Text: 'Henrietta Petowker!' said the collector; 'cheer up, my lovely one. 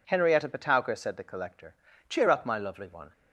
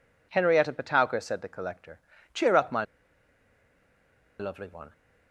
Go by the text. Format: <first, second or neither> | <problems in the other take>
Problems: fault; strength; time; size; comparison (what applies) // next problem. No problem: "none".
first | pauses between "my" and "lovely"; strong; at 2.8 s; 1.5 s long